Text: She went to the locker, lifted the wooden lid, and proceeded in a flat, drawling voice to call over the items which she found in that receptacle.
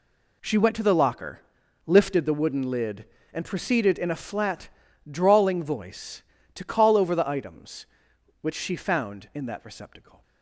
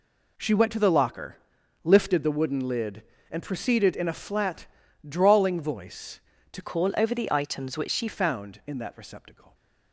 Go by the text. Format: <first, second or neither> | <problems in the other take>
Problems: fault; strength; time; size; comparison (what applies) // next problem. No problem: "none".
first | changes voice from "call" to "she"; from 6.6 to 8.0 s; 1.4 s long